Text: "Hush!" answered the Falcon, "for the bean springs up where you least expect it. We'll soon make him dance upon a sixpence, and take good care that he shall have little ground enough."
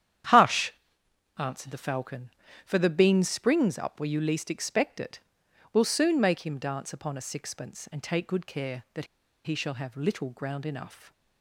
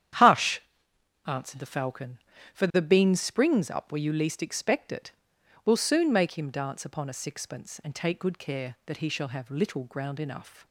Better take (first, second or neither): second